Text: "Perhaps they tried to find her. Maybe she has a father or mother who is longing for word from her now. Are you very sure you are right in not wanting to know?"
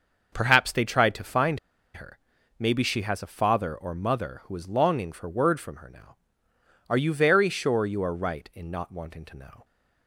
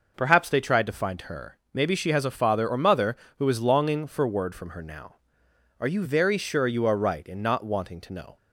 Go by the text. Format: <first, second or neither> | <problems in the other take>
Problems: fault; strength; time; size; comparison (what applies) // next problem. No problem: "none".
second | starts louder than the rest; until 1.3 s; 6.5 dB // pauses between "find" and "her"; slight; at 1.5 s; 0.35 s long